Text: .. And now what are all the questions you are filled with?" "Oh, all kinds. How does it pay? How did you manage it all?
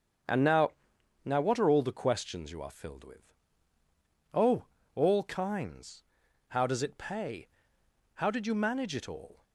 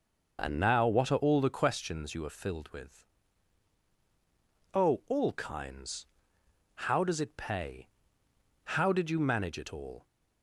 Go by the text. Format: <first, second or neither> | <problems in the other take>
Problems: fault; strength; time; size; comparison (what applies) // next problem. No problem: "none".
second | starts louder than the rest; strong; until 1.7 s; 7.5 dB // says "now" twice; at 1.2 s